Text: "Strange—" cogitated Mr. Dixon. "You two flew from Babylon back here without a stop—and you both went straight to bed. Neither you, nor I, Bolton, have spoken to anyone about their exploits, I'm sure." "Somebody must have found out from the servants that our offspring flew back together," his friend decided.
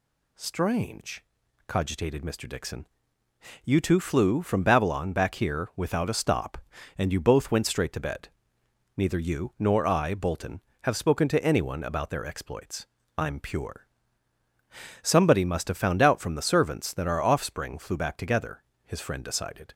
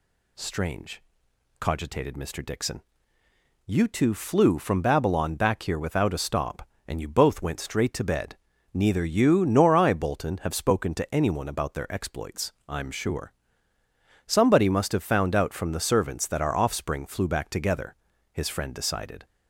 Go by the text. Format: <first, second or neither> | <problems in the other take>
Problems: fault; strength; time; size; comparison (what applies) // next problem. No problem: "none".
second | says "pure" for "sure"; at 13.3 s